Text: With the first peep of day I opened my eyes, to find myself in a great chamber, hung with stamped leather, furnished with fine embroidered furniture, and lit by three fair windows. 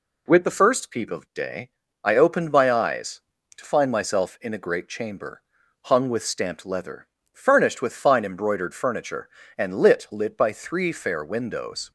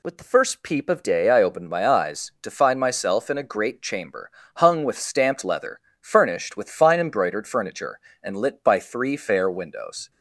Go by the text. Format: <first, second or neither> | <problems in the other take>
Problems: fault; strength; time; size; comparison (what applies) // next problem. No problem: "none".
second | pauses between "day" and "I"; slight; at 1.6 s; 0.34 s long // says "lit" twice; at 10.1 s